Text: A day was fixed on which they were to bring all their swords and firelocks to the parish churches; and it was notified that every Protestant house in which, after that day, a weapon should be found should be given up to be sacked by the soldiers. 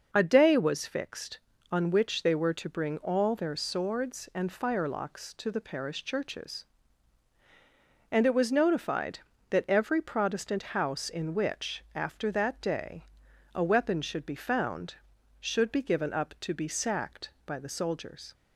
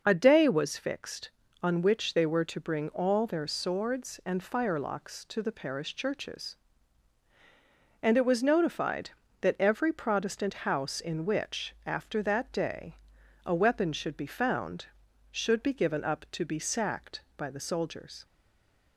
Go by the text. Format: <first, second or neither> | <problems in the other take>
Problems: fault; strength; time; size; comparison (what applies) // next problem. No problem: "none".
first | stays silent after the last word; slight; from 18.2 s on; 0.7 s long